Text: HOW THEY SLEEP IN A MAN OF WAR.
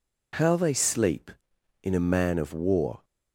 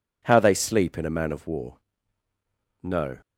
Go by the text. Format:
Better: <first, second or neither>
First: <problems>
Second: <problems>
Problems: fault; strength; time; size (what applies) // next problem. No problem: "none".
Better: first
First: none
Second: goes on to say "No"; slight; from 2.8 s on; 0.36 s long